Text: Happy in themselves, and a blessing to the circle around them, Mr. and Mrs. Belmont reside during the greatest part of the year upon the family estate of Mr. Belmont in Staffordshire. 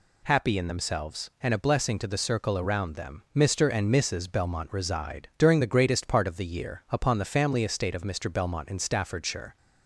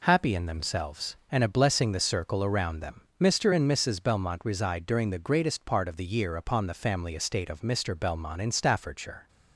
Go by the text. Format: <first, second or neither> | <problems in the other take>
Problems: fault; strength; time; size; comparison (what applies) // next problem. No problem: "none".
first | skips "to"; at 1.9 s